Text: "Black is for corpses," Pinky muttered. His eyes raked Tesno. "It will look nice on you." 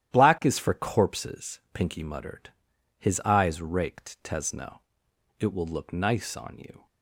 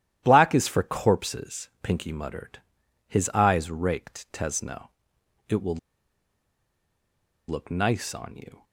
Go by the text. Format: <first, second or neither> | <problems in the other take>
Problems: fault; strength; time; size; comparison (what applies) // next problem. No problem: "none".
first | starts louder than the rest; strong; until 1.2 s; 11.5 dB; strong in the first // pauses between "will" and "look"; strong; at 5.7 s; 1.7 s long